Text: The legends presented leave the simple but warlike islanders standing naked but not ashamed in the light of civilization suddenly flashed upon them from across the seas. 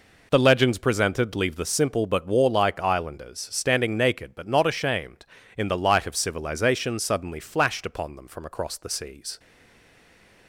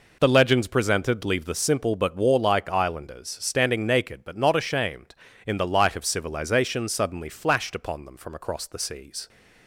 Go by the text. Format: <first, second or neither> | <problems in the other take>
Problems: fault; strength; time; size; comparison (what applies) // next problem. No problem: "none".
second | stays silent after the last word; from 9.3 s on; 1.1 s long